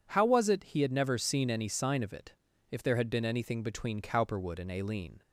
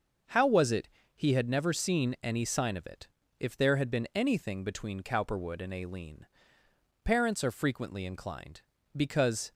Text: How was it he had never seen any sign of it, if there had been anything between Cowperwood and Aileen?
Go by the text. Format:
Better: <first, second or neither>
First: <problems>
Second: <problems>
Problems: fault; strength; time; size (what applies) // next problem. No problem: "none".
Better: first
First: none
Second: starts louder than the rest; until 1.5 s; 6 dB // pauses between "it" and "he"; slight; at 0.8 s; 0.28 s long // goes on to say "Parents are frequently inclined because"; strong; from 7.0 s on; 2.5 s long